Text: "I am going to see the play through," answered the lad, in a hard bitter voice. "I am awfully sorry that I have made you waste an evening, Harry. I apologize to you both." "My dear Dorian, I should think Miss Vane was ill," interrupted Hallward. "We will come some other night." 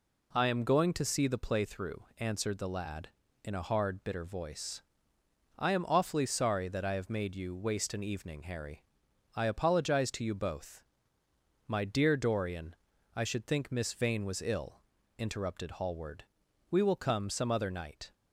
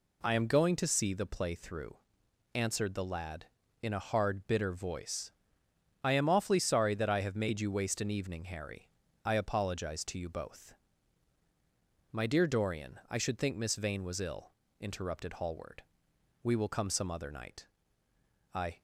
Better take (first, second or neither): first